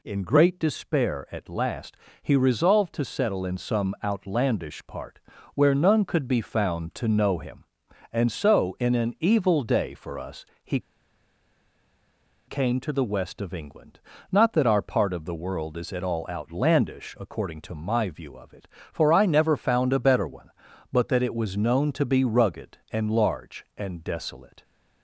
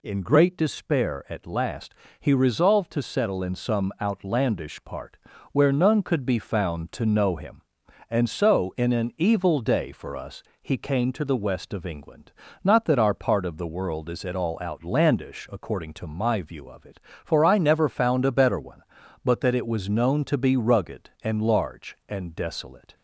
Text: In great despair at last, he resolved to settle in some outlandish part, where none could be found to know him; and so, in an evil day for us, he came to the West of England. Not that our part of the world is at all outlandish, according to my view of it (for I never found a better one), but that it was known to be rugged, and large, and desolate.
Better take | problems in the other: second | pauses between "he" and "came"; strong; at 10.7 s; 1.6 s long

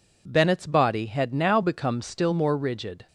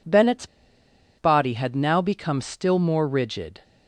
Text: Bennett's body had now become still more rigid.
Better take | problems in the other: first | pauses between "Bennett's" and "body"; noticeable; at 0.4 s; 0.72 s long

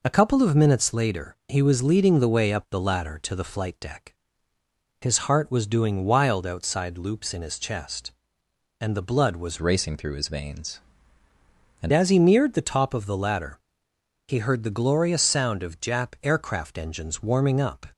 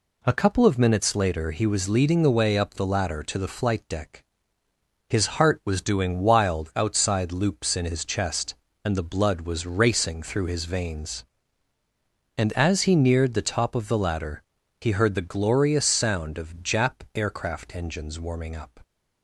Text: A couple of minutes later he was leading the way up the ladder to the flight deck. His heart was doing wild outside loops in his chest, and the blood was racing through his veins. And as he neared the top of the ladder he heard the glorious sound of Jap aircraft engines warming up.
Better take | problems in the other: second | changes voice from "racing" to "And"; from 9.6 to 11.9 s; 2.3 s long // pauses between "ladder" and "he"; noticeable; at 13.6 s; 0.66 s long; also in the second

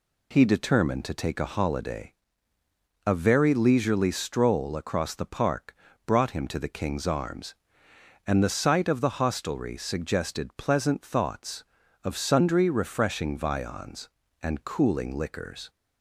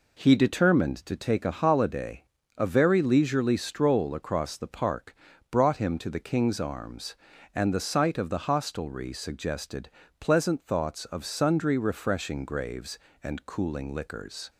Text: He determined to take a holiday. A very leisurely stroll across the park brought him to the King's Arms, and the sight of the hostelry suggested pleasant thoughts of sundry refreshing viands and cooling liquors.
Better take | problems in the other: first | pauses between "park" and "brought"; at 5.1 s; 0.38 s long; slight in the first // pauses between "suggested" and "pleasant"; slight; at 9.8 s; 0.28 s long // says "graves" for "viands"; at 12.4 s

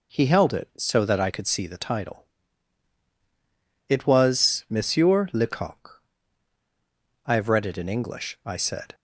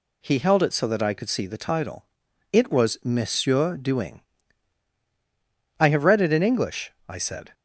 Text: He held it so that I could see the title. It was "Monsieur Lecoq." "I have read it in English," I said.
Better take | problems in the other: first | says "Duing" for "Lecoq"; at 3.7 s

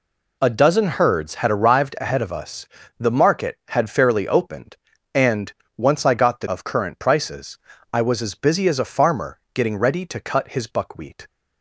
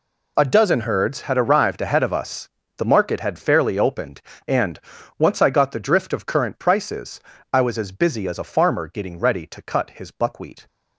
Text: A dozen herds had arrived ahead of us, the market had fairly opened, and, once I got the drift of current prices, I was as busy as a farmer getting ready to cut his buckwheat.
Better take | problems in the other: second | skips "drift"; at 6.4 s

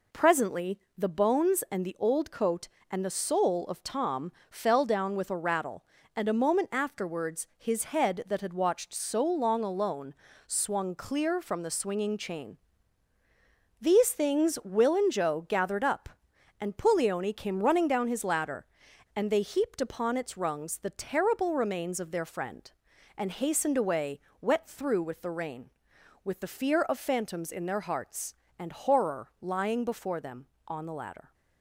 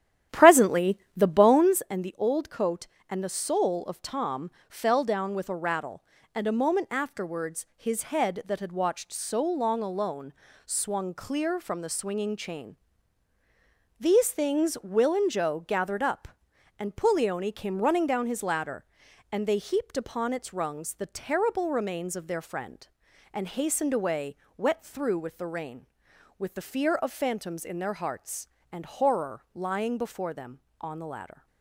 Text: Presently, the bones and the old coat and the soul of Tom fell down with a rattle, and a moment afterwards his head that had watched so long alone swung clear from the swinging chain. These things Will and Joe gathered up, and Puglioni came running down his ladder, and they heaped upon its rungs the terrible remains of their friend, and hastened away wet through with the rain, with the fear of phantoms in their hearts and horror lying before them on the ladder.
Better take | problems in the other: first | starts louder than the rest; strong; until 1.9 s; 11.5 dB // pauses between "Tom" and "fell"; slight; at 4.5 s; 0.18 s long; slight in the first // pauses between "alone" and "swung"; slight; at 10.3 s; 0.34 s long; slight in the first // pauses between "away" and "wet"; slight; at 24.3 s; 0.22 s long; slight in the first

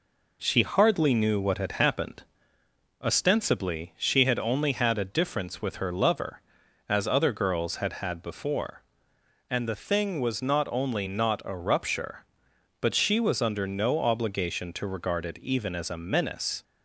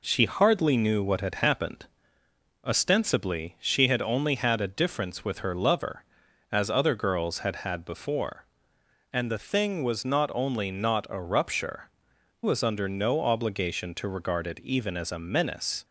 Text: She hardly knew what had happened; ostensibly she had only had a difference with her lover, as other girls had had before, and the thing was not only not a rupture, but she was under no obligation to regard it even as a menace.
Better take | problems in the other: first | skips "but she"; at 12.1 s

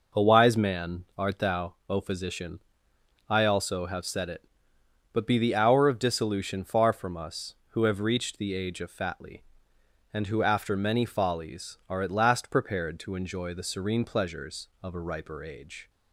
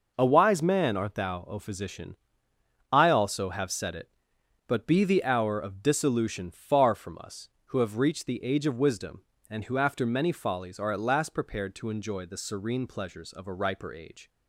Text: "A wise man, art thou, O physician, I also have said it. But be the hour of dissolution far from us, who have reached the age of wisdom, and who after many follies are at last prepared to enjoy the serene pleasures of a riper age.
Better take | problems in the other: second | says "fatly" for "wisdom"; at 8.9 s

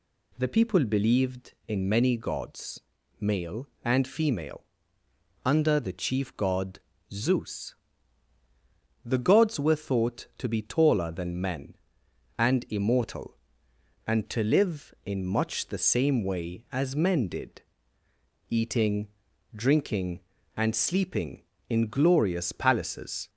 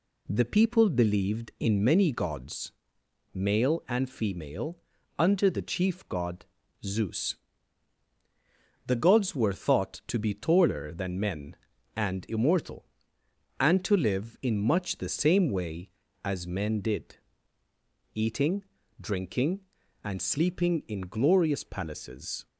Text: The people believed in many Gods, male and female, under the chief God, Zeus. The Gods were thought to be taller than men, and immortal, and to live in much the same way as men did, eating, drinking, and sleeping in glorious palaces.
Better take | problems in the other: neither | none

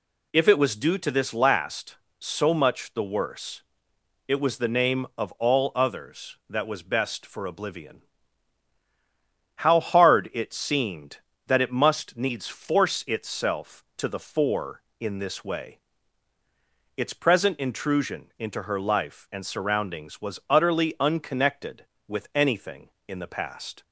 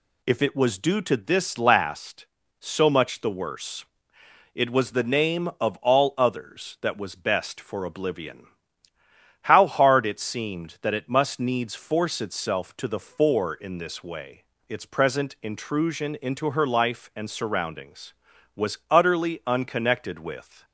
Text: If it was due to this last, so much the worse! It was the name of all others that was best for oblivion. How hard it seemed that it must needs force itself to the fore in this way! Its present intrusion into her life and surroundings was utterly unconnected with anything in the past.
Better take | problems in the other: first | stops before "anything in the past"; at 20.6 s

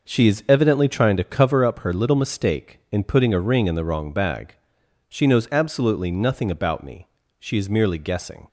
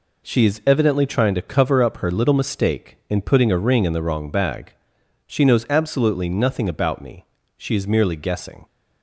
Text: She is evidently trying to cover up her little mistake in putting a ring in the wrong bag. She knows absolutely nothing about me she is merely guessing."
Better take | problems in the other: second | starts louder than the rest; noticeable; until 1.7 s; 6 dB // pauses between "me" and "she"; slight; at 7.0 s; 0.30 s long; slight in the second

